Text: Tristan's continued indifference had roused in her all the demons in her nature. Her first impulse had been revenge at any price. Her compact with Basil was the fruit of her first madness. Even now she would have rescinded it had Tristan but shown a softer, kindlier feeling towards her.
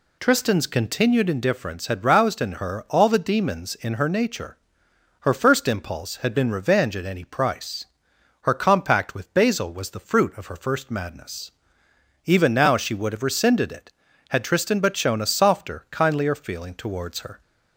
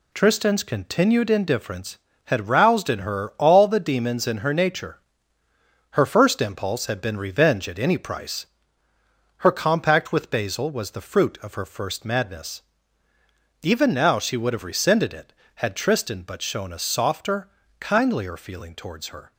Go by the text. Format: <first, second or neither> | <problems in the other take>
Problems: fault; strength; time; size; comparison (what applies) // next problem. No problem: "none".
neither | none